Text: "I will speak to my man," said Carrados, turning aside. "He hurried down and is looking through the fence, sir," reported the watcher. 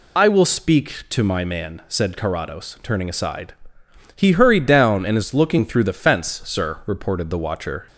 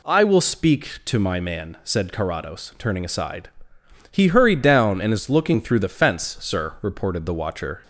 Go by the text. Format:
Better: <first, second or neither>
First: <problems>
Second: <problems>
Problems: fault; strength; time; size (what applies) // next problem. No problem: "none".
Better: second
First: loses the start of "I"; at 0.1 s; 75 ms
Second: none